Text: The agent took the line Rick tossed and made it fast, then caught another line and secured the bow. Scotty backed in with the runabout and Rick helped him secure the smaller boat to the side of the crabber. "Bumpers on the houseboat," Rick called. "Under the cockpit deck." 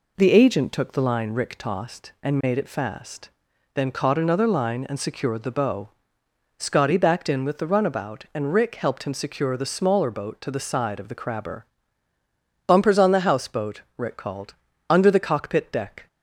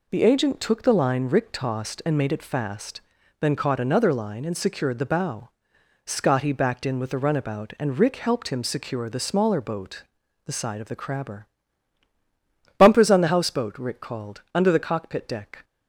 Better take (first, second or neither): first